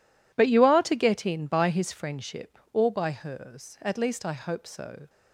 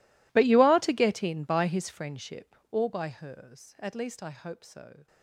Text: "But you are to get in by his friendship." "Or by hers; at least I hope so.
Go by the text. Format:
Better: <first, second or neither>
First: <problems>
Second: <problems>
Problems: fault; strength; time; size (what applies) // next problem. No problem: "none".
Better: first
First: none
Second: gets quieter; strong; throughout; 24.5 dB